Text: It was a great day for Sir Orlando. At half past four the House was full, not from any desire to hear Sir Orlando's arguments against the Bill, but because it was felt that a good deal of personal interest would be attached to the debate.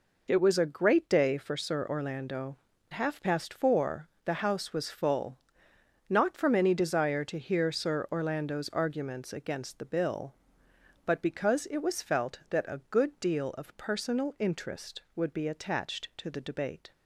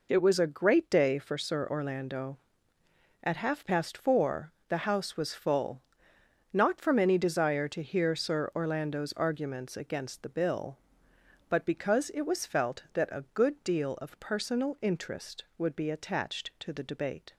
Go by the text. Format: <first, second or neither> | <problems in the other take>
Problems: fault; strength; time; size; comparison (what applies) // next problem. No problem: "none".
second | skips "At"; at 2.7 s // pauses between "four" and "the"; slight; at 4.0 s; 0.18 s long; slight in the second